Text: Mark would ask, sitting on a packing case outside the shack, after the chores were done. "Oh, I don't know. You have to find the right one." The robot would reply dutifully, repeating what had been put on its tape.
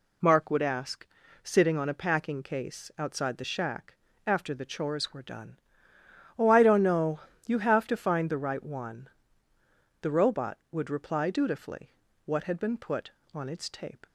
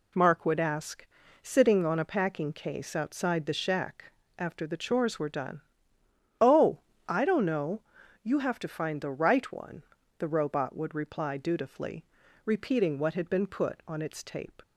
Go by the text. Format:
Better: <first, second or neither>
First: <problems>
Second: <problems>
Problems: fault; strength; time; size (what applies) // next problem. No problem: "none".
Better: second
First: skips "repeating"; at 12.0 s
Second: none